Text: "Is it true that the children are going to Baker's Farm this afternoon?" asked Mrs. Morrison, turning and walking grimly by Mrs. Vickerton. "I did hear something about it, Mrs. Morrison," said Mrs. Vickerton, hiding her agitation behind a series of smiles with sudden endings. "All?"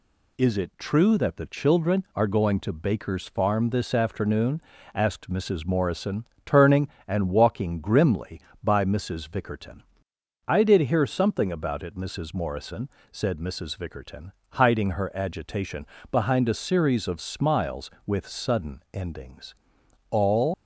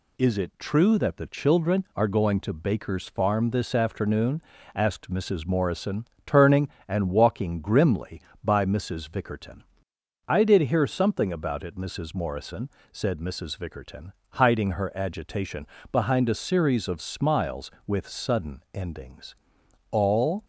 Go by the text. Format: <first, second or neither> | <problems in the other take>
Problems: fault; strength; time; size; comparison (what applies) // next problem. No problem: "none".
second | pauses between "agitation" and "behind"; slight; at 15.8 s; 0.26 s long; slight in the second // leaves "All" unfinished; at 20.5 s; 100 ms